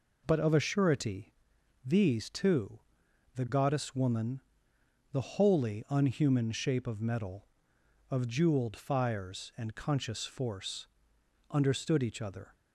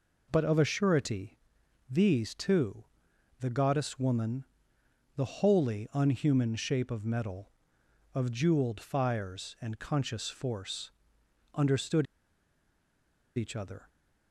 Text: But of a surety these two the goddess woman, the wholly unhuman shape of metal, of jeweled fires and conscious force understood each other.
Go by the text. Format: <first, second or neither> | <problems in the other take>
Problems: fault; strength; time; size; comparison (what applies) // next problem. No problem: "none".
first | pauses between "surety" and "these"; noticeable; at 1.3 s; 0.52 s long; noticeable in the first // pauses between "two" and "the"; noticeable; at 2.8 s; 0.56 s long; noticeable in the first // pauses between "force" and "understood"; noticeable; at 10.8 s; 0.64 s long; noticeable in the first // pauses between "understood" and "each"; strong; at 12.0 s; 1.3 s long